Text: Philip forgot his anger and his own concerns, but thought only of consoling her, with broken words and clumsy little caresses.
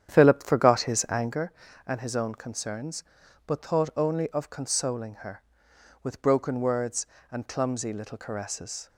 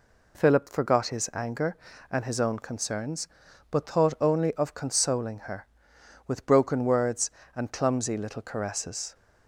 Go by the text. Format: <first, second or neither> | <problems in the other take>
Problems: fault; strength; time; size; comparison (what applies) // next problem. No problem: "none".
second | starts louder than the rest; strong; until 1.4 s; 9.5 dB